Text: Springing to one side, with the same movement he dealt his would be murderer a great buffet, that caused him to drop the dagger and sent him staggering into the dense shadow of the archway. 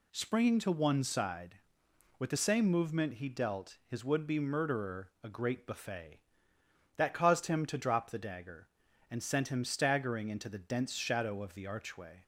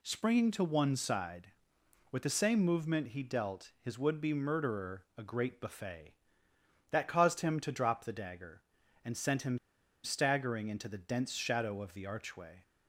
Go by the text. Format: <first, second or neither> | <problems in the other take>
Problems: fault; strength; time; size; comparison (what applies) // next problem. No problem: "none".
first | pauses between "him" and "staggering"; at 9.5 s; 0.45 s long